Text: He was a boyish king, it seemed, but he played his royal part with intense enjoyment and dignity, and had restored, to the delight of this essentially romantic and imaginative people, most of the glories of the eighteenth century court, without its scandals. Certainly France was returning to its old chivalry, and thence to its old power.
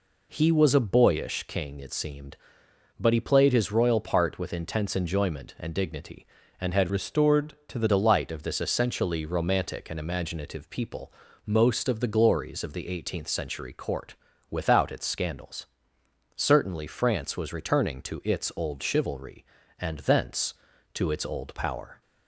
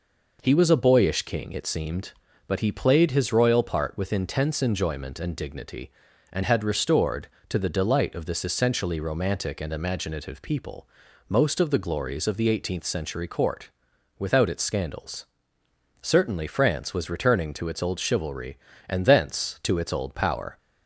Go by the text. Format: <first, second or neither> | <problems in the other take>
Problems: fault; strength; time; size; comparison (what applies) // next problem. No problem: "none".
second | changes voice from "restored" to "the"; from 6.8 to 7.8 s; 1.0 s long